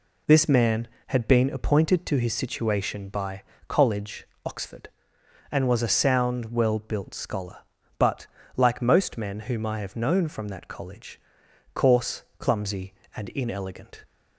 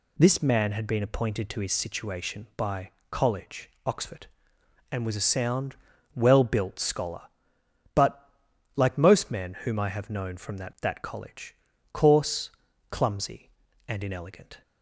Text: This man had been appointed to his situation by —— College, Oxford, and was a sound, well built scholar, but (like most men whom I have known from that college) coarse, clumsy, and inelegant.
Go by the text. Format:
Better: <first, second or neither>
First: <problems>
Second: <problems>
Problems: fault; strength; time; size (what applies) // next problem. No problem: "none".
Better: first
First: none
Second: says "that" twice; at 10.8 s